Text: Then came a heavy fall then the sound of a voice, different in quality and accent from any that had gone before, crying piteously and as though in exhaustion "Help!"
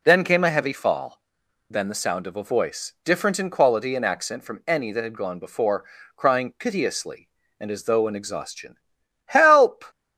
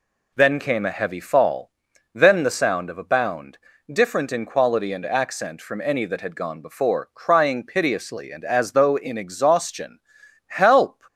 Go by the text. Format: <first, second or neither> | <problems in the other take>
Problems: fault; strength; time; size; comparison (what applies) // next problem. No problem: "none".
first | pauses between "fall" and "then"; at 1.7 s; 0.44 s long; noticeable in the first // says "bound" for "voice"; at 3.0 s // pauses between "exhaustion" and "Help"; noticeable; at 9.9 s; 0.48 s long; noticeable in the first